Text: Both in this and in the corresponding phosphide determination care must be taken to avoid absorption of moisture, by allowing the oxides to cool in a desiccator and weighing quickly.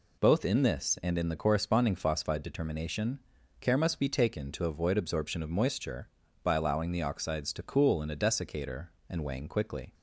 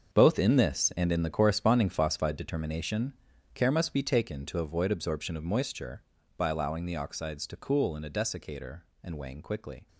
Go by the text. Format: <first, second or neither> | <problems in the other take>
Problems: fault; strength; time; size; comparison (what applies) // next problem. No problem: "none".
first | gets quieter; strong; throughout; 13 dB // pauses between "determination" and "care"; at 3.1 s; 0.40 s long; also in the first